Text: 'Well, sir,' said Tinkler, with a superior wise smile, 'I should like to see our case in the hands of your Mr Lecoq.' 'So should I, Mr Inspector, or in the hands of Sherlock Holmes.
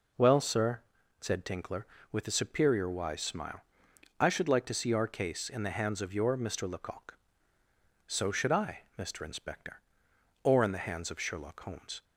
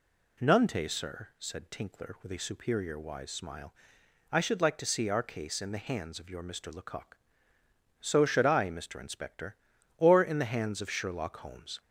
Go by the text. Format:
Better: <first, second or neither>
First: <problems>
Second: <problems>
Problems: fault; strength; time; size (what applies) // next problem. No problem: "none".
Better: first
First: none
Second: says "Nunte" for "Well"; at 0.3 s